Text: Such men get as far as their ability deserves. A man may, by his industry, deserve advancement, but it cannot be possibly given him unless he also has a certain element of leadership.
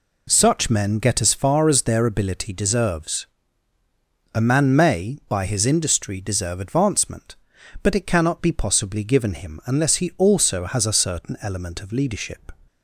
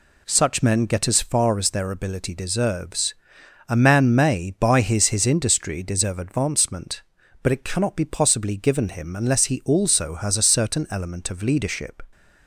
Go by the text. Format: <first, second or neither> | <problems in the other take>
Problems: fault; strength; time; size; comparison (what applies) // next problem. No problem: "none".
first | says "his" twice; at 5.0 s